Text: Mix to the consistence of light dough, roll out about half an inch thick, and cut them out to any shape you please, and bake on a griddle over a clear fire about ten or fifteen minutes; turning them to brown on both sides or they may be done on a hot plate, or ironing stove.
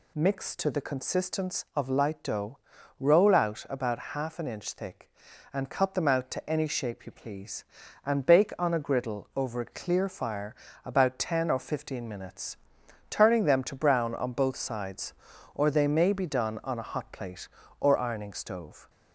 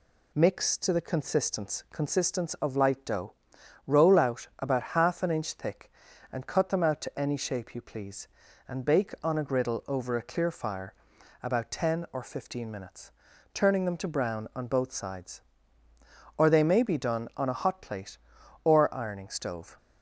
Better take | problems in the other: first | says "consistence" twice; at 1.9 s // pauses between "fire" and "about"; noticeable; at 10.9 s; 0.50 s long; slight in the first

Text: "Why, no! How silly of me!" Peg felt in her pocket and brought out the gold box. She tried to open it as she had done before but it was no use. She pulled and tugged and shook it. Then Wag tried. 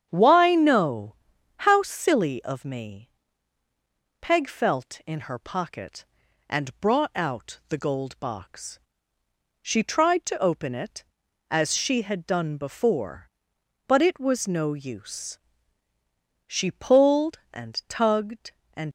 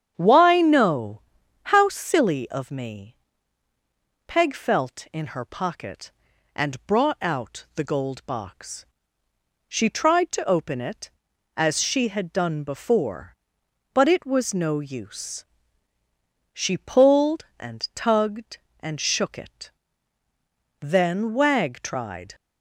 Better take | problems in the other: second | starts louder than the rest; strong; until 1.1 s; 8.5 dB; strong in the second // stops before "shook it Then Wag tried"; at 18.8 s

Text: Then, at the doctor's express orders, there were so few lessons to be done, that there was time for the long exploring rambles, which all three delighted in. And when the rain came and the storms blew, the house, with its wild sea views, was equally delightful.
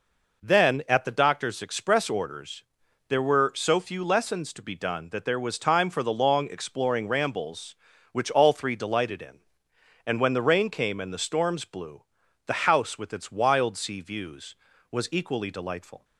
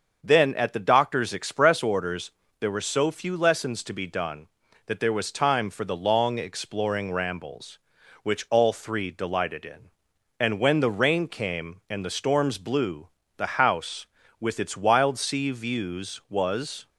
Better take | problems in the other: first | starts louder than the rest; until 1.2 s; 6.5 dB // stops before "equally delightful"; at 16.8 s

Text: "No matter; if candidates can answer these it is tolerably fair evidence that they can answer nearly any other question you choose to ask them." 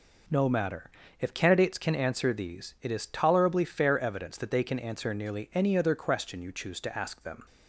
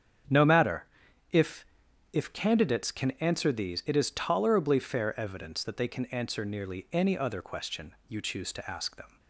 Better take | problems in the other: first | starts louder than the rest; strong; until 2.2 s; 8 dB // says "if" twice; at 2.1 s

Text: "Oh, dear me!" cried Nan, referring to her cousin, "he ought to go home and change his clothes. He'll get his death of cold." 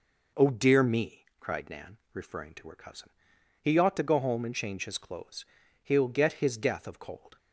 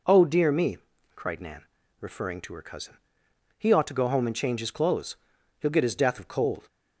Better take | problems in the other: neither | none

